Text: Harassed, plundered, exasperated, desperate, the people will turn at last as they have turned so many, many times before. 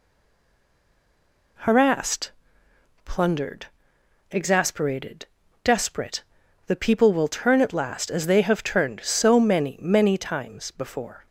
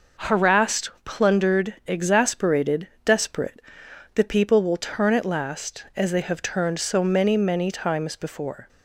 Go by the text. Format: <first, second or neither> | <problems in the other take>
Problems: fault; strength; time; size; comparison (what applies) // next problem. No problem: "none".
second | stays silent before the first word; noticeable; until 1.5 s; 1.5 s long